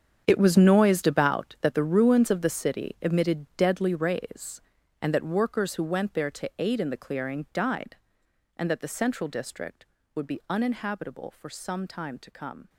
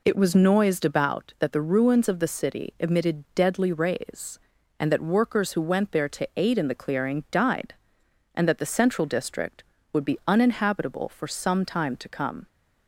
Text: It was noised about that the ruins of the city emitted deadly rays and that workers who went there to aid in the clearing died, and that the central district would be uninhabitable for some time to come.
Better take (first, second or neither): second